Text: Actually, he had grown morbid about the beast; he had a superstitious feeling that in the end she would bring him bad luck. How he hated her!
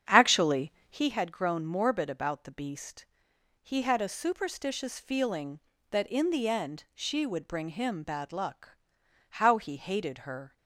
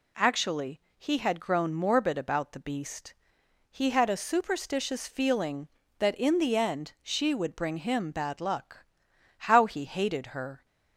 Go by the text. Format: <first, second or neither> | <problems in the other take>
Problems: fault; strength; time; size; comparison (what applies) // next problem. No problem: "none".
second | starts louder than the rest; strong; until 1.1 s; 8 dB